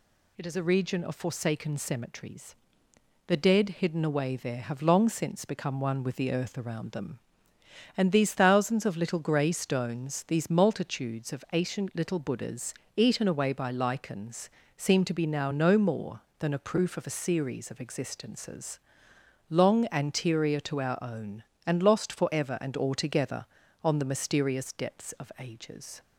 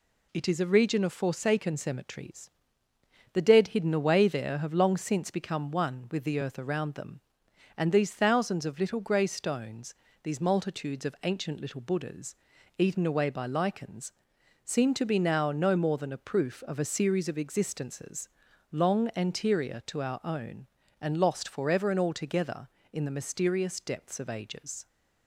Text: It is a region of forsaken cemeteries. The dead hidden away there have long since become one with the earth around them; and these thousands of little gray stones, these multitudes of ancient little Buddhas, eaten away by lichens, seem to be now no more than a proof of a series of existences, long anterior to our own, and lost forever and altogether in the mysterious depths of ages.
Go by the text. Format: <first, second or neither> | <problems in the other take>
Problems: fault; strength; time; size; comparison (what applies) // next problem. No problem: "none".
second | says "on" for "in"; at 23.8 s